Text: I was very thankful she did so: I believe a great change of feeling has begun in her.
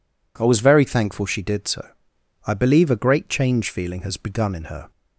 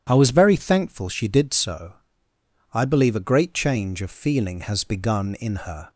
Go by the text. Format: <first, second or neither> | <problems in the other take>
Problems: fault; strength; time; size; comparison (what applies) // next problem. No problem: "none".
second | skips "of"; at 3.7 s